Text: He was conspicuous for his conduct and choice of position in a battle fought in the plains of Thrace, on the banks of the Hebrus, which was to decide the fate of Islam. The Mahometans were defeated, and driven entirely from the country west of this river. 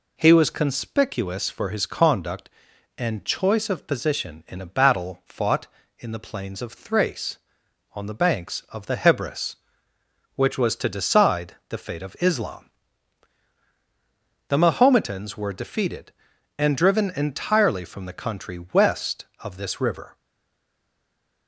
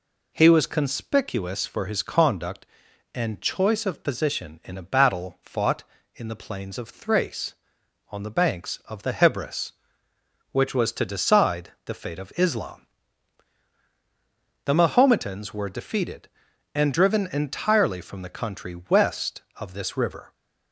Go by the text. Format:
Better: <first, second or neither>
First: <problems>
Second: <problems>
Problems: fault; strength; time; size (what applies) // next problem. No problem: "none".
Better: second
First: stays silent after the last word; noticeable; from 20.1 s on; 1.3 s long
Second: none